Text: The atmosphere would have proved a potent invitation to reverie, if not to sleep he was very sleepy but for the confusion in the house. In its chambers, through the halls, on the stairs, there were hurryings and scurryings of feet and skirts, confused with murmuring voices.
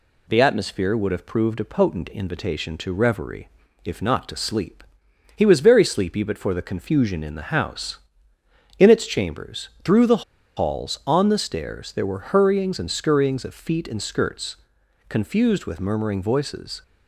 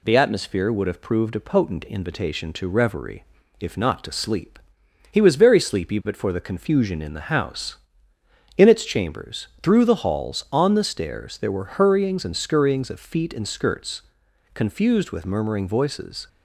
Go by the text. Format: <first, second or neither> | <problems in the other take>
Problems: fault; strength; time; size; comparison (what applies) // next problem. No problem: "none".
second | pauses between "sleep" and "he"; noticeable; at 4.8 s; 0.54 s long; noticeable in the second // pauses between "the" and "halls"; slight; at 10.2 s; 0.33 s long